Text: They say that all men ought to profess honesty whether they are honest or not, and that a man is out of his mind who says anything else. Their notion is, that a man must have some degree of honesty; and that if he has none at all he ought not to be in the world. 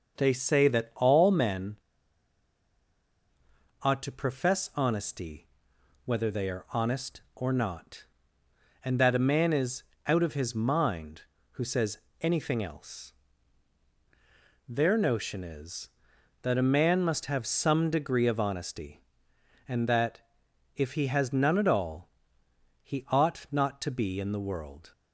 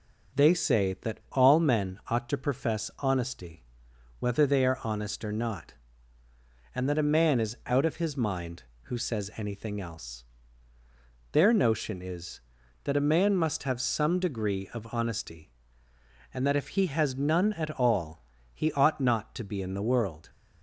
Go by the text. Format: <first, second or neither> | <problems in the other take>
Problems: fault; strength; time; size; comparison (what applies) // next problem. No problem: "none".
second | pauses between "men" and "ought"; strong; at 1.7 s; 2.0 s long // pauses between "honesty" and "whether"; noticeable; at 5.4 s; 0.58 s long; noticeable in the second // pauses between "is" and "out"; slight; at 9.8 s; 0.24 s long // pauses between "says" and "anything"; slight; at 11.9 s; 0.24 s long // pauses between "that" and "if"; noticeable; at 20.1 s; 0.56 s long // pauses between "all" and "he"; noticeable; at 22.0 s; 0.76 s long; slight in the second